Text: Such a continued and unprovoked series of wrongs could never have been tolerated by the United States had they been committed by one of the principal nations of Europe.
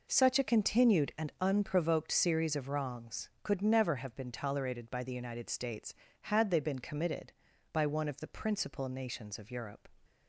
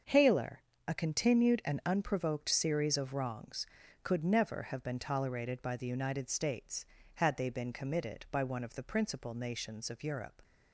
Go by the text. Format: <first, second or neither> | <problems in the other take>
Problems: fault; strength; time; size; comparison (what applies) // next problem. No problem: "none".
first | starts louder than the rest; until 1.3 s; 6.5 dB // says "Haler" for "Such"; at 0.0 s